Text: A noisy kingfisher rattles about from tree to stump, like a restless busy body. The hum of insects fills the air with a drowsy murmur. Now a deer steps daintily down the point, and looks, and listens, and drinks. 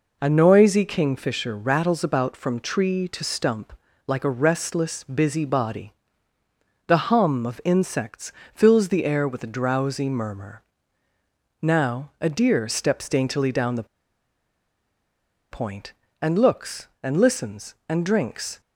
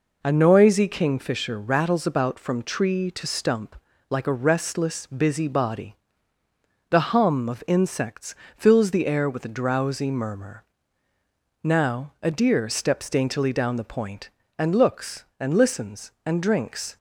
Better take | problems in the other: second | pauses between "insects" and "fills"; slight; at 8.3 s; 0.20 s long; slight in the second // pauses between "the" and "point"; strong; at 13.8 s; 1.6 s long

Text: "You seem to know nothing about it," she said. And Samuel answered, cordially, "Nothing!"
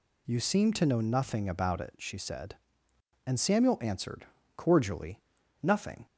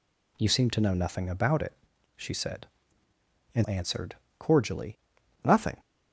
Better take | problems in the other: first | skips "Samuel"; at 3.6 s

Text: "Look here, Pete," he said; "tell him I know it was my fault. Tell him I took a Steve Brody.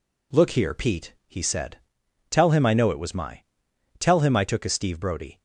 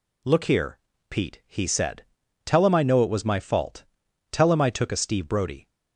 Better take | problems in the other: second | skips "fault"; at 3.7 s

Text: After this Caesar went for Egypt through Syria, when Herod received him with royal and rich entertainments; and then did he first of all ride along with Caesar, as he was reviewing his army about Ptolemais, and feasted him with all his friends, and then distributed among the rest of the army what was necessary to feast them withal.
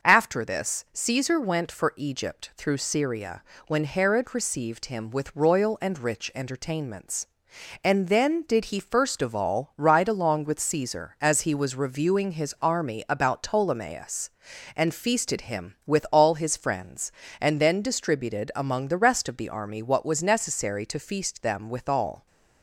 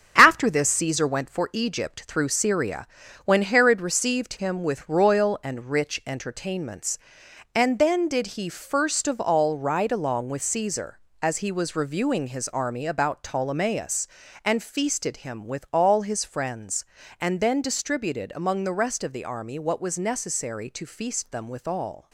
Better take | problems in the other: first | gets quieter; throughout; 6.5 dB

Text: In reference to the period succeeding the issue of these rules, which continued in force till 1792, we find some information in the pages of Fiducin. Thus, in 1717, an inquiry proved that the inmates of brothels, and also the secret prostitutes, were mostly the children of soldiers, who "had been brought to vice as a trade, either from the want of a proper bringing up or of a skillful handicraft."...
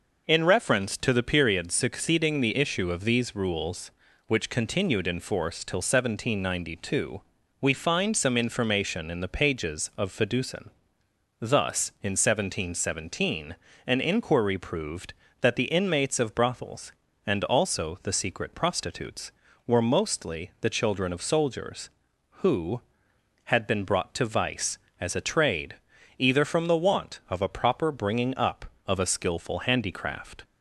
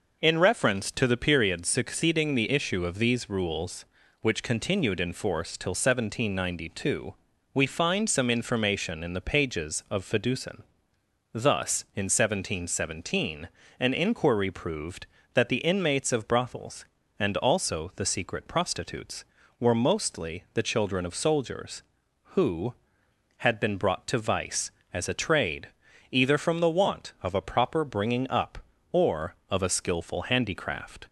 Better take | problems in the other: second | skips "or"; at 28.7 s

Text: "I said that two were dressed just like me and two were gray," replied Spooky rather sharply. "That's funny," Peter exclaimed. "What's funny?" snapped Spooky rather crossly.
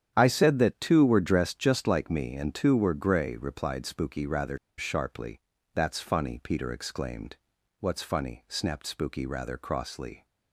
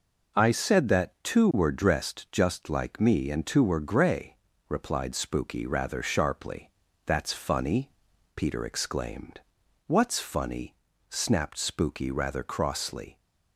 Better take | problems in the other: second | starts louder than the rest; strong; until 1.1 s; 9.5 dB // pauses between "rather" and "sharply"; slight; at 4.5 s; 0.21 s long

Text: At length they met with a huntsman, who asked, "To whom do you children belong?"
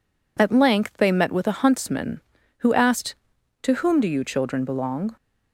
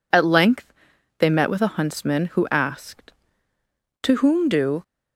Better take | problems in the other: first | pauses between "length" and "they"; noticeable; at 0.7 s; 0.46 s long // stops before "you children belong"; at 4.8 s

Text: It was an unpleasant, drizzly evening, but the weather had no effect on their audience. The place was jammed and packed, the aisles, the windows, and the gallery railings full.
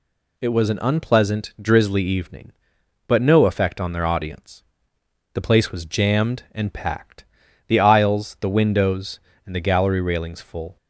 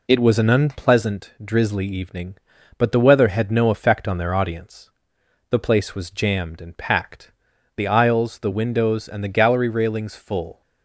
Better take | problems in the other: second | skips "the weather had"; at 3.2 s

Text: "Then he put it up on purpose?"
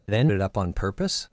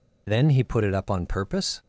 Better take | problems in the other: second | skips "he put"; at 0.3 s

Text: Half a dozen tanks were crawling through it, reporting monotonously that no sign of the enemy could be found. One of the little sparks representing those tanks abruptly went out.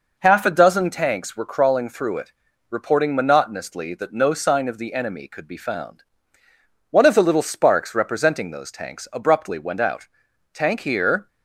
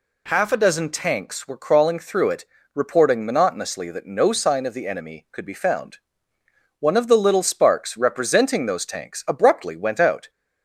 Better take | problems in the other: second | goes on to say "Tank here"; noticeable; from 10.5 s on; 0.74 s long

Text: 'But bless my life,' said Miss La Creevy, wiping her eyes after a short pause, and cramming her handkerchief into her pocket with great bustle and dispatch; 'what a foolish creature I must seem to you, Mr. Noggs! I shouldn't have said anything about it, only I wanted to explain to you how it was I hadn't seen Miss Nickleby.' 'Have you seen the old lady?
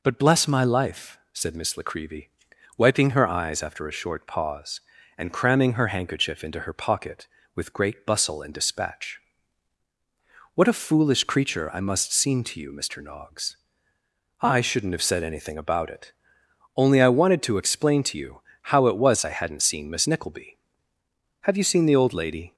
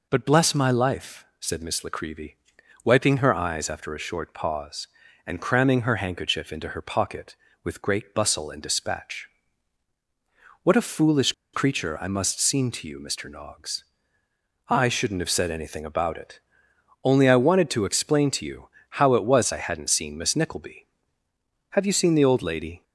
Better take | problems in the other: first | pauses between "foolish" and "creature"; slight; at 11.3 s; 0.21 s long // pauses between "you" and "how"; slight; at 18.6 s; 0.22 s long; slight in the first

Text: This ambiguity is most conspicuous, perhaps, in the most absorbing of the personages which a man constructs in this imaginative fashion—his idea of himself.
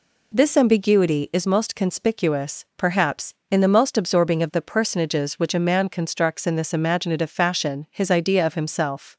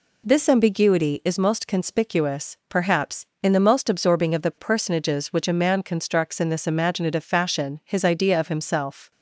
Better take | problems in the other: neither | none

